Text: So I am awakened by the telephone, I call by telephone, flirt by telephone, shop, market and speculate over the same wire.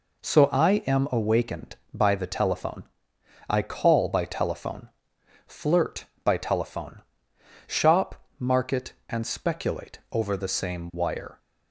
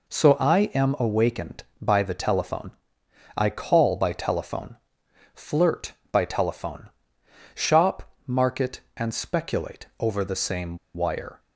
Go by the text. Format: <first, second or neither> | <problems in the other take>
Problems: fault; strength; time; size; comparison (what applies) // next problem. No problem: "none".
first | pauses between "same" and "wire"; slight; at 10.7 s; 0.17 s long